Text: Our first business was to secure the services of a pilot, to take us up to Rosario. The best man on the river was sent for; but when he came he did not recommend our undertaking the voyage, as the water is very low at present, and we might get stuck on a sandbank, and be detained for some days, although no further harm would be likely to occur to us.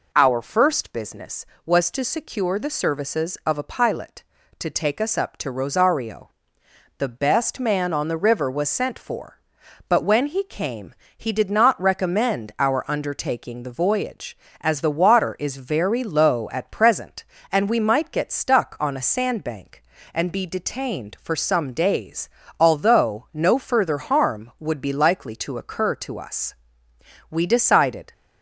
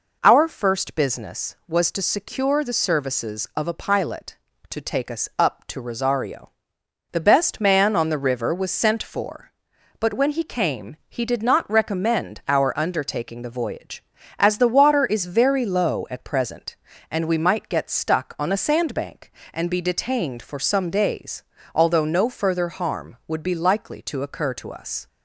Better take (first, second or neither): second